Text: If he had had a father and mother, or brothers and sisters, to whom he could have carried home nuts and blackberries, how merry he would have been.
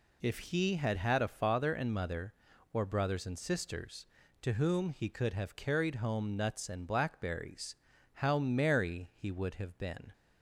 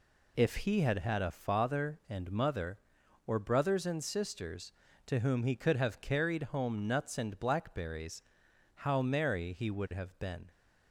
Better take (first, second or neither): neither